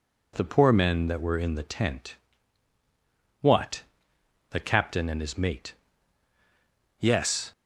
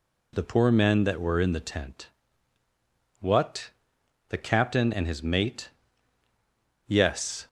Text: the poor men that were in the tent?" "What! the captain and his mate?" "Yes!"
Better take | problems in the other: neither | none

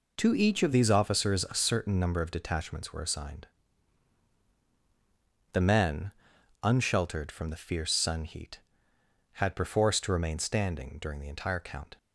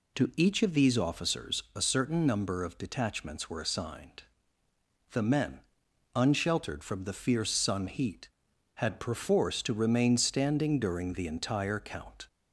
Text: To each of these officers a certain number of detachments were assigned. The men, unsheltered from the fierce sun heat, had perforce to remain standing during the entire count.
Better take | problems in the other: second | changes voice at "these"; from 0.7 s on; 11.2 s long

